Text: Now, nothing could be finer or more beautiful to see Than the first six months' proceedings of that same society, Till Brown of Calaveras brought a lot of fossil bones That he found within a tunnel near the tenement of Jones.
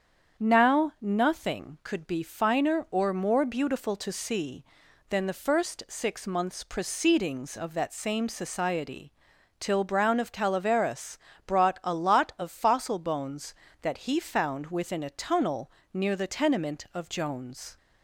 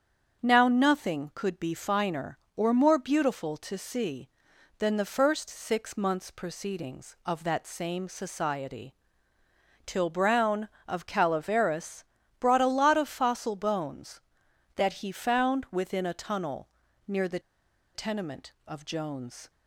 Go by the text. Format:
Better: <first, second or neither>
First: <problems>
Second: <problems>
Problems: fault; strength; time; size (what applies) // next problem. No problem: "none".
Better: first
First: starts louder than the rest; strong; until 1.4 s; 8 dB // pauses between "Calaveras" and "brought"; slight; at 11.1 s; 0.28 s long // pauses between "tunnel" and "near"; slight; at 15.6 s; 0.22 s long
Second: starts louder than the rest; strong; until 1.4 s; 8 dB // pauses between "Calaveras" and "brought"; slight; at 12.0 s; 0.36 s long // pauses between "tunnel" and "near"; at 16.6 s; 0.40 s long // pauses between "the" and "tenement"; noticeable; at 17.3 s; 0.55 s long